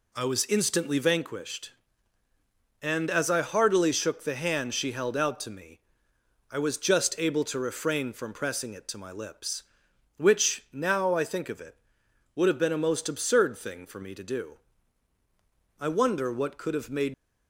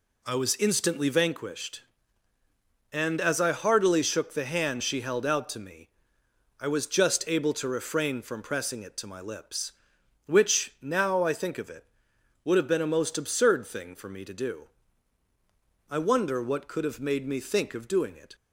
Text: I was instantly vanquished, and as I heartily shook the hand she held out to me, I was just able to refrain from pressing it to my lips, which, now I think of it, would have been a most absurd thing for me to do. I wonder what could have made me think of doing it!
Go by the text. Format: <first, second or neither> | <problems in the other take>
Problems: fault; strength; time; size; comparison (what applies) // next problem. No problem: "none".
second | stops before "me think of doing it"; at 17.1 s